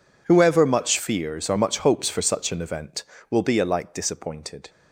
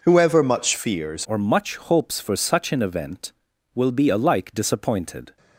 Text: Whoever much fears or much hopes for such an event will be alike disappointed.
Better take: first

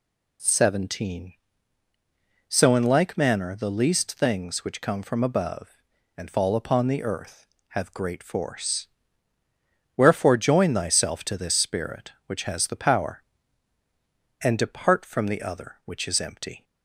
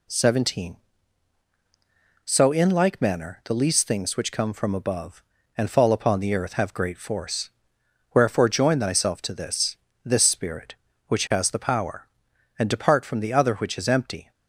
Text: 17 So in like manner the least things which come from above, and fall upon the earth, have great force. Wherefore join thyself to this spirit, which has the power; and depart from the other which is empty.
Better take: first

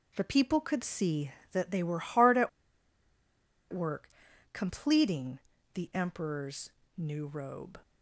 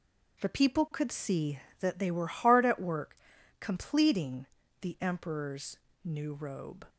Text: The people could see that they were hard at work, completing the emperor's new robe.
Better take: second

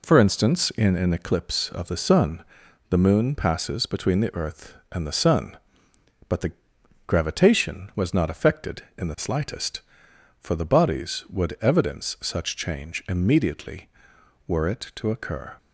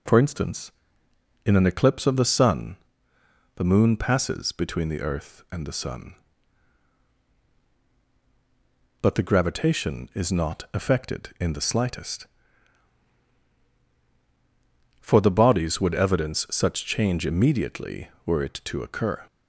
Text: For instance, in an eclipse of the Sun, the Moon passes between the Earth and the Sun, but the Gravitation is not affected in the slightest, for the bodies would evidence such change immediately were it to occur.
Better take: second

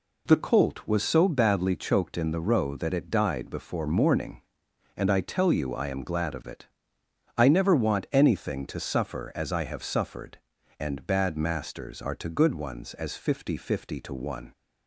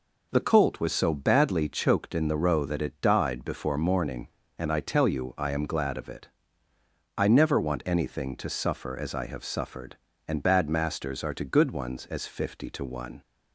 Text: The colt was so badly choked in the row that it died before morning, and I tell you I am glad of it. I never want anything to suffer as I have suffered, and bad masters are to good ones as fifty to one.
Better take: second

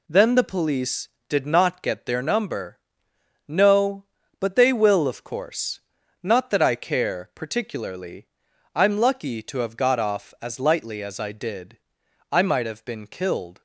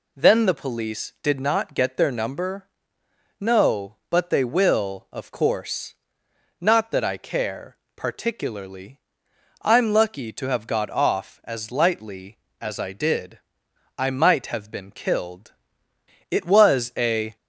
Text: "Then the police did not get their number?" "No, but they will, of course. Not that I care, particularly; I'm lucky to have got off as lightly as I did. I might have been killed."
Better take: first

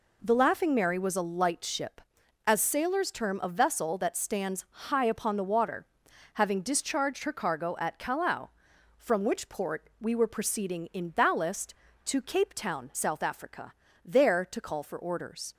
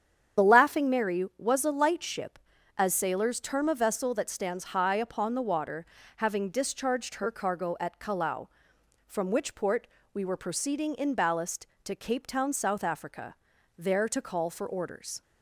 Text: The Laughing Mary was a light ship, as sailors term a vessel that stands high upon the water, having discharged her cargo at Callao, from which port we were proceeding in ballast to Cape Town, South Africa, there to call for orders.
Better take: first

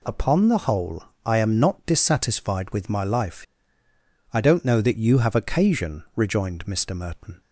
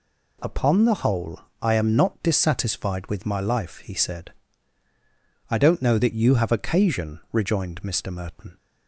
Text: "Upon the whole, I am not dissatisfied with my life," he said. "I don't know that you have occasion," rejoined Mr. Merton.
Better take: second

